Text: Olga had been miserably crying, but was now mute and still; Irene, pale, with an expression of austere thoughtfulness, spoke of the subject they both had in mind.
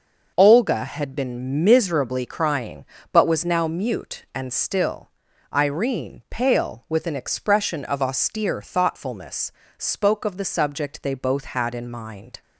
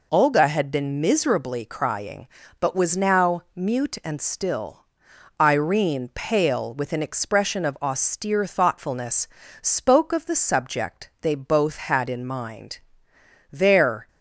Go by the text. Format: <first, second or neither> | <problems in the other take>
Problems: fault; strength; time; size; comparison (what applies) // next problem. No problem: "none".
first | goes on to say "There"; from 13.5 s on; 0.56 s long